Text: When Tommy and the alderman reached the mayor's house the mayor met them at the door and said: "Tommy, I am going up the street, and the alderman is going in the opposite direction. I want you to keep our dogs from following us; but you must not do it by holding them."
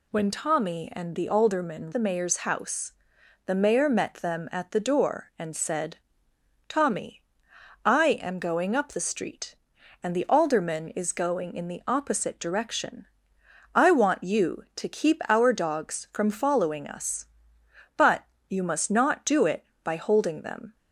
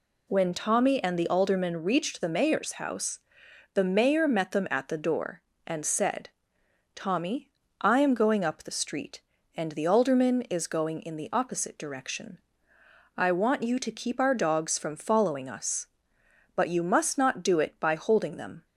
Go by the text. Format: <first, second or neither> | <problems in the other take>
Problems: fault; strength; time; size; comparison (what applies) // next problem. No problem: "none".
second | skips "reached"; at 1.9 s // pauses between "house" and "the"; noticeable; at 2.9 s; 0.56 s long; noticeable in the second // pauses between "but" and "you"; slight; at 18.2 s; 0.26 s long